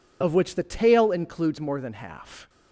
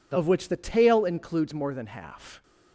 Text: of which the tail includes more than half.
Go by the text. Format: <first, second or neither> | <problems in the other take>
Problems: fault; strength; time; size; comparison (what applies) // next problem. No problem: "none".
second | loses the start of "of"; at 0.2 s; 25 ms